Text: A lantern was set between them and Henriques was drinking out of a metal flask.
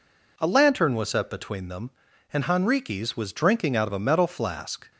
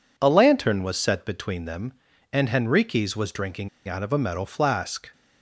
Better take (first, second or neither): first